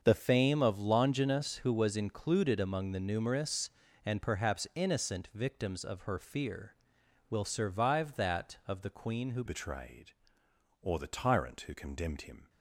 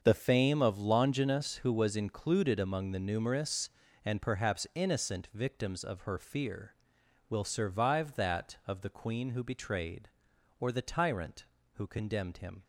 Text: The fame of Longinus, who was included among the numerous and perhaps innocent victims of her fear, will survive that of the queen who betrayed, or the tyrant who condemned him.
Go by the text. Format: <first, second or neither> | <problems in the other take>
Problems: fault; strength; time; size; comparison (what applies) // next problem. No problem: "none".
second | starts louder than the rest; until 1.0 s; 6.5 dB; also in the second // changes voice at "betrayed"; from 9.4 s on; 3.0 s long